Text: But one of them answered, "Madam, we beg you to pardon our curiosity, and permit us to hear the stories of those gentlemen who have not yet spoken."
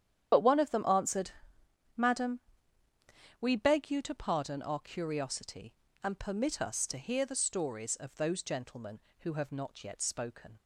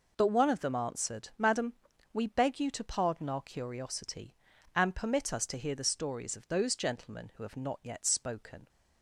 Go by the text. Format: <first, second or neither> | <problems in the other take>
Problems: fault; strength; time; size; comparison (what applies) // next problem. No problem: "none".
second | loses the start of "But"; at 0.3 s; 50 ms // starts louder than the rest; strong; until 1.9 s; 9.5 dB